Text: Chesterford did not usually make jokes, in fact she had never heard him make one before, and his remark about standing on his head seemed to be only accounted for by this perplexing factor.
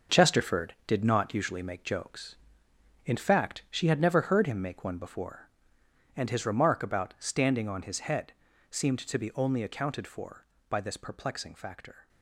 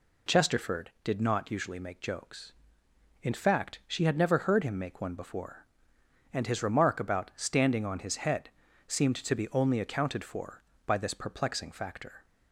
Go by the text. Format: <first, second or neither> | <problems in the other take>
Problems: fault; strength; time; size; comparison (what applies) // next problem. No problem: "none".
second | gets quieter; strong; throughout; 10 dB // pauses between "head" and "seemed"; at 8.3 s; 0.40 s long; also in the second